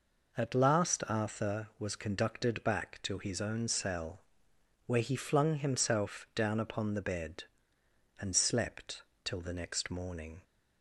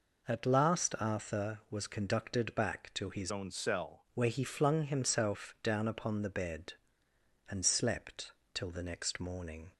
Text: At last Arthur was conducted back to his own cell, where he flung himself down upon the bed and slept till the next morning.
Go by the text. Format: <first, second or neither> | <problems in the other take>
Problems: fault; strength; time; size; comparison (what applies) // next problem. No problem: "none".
first | changes voice from "own" to "cell"; from 3.3 to 4.0 s; 0.7 s long // pauses between "slept" and "till"; slight; at 8.3 s; 0.22 s long; slight in the first